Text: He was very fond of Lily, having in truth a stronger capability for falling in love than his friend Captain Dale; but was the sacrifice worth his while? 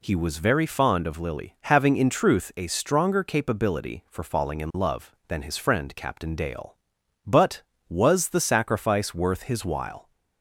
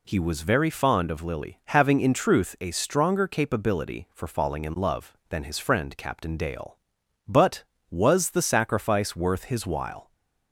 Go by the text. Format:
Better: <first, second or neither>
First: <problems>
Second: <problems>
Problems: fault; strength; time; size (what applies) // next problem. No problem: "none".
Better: neither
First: none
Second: none